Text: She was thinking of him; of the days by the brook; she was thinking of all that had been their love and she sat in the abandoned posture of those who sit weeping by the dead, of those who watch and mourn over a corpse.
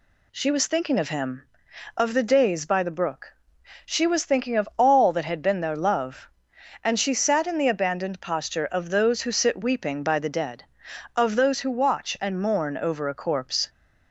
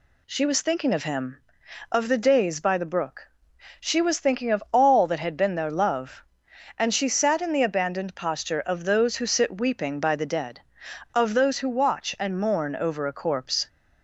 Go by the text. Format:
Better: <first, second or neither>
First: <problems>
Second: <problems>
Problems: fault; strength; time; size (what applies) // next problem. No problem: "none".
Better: neither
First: none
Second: none